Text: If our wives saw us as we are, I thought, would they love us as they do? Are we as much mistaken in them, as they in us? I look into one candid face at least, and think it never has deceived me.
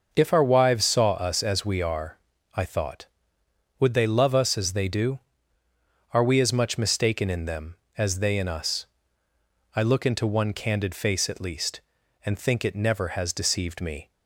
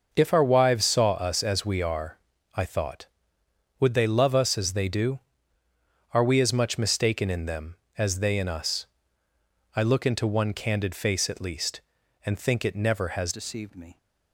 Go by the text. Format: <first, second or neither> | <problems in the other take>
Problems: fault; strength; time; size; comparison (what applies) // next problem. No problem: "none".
first | starts louder than the rest; until 1.1 s; 6 dB; also in the first // changes voice at "deceived"; from 13.3 s on; 0.6 s long